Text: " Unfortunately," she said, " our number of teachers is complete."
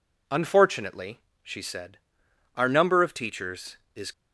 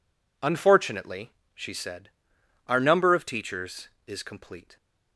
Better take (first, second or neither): second